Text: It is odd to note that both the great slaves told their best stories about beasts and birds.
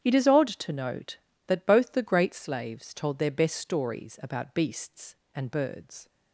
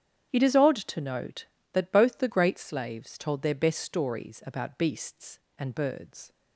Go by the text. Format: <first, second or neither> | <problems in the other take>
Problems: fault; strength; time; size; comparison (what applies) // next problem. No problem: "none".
neither | starts louder than the rest; strong; the same in both